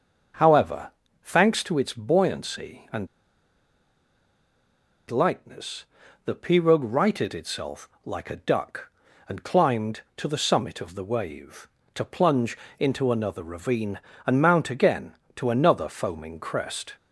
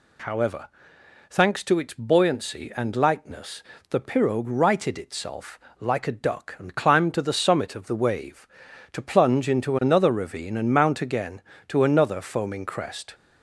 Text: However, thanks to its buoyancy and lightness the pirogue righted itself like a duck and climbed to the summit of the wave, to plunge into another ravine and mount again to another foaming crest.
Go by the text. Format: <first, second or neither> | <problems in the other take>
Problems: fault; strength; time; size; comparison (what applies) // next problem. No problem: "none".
second | starts louder than the rest; until 1.7 s; 6.5 dB // pauses between "and" and "lightness"; strong; at 3.0 s; 2.0 s long // pauses between "lightness" and "the"; at 5.8 s; 0.40 s long; slight in the second // pauses between "itself" and "like"; slight; at 7.8 s; 0.16 s long; slight in the second // pauses between "plunge" and "into"; slight; at 12.5 s; 0.20 s long